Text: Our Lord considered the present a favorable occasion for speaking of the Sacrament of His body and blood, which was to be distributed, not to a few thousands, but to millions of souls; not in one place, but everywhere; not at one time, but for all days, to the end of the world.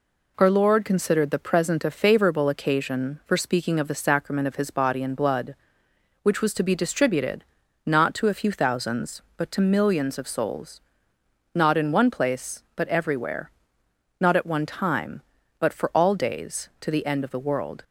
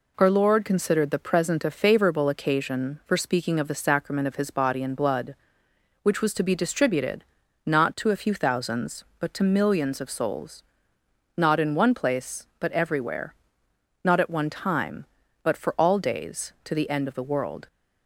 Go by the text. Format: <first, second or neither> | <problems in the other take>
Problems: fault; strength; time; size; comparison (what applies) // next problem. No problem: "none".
neither | none